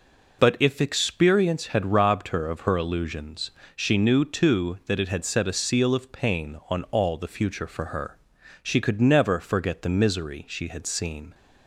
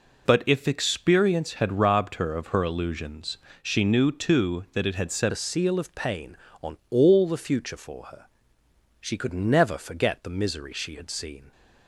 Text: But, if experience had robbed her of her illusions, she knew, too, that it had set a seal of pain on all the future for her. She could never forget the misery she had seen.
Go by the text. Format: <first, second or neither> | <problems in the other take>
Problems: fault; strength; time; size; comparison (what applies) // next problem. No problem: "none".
first | changes voice at "a"; from 5.3 s on; 6.2 s long